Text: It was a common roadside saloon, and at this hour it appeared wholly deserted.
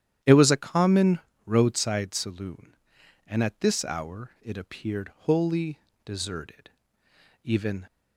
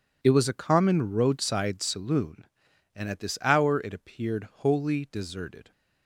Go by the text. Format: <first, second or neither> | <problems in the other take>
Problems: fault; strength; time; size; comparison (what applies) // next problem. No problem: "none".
second | starts louder than the rest; strong; until 1.5 s; 10.5 dB // pauses between "common" and "roadside"; slight; at 1.1 s; 0.28 s long // pauses between "wholly" and "deserted"; slight; at 5.7 s; 0.26 s long // goes on to say "Even"; slight; from 7.4 s on; 0.42 s long